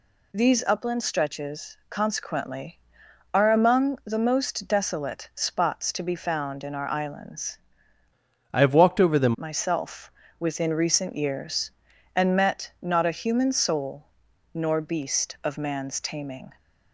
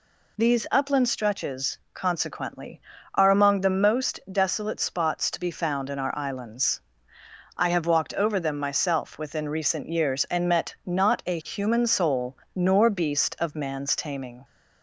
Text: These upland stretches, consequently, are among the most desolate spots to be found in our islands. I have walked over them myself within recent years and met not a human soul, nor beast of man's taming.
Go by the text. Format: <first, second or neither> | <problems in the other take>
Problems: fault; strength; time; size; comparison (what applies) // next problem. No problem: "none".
second | changes voice from "I" to "them"; from 8.5 to 9.3 s; 0.8 s long // pauses between "myself" and "within"; slight; at 10.1 s; 0.26 s long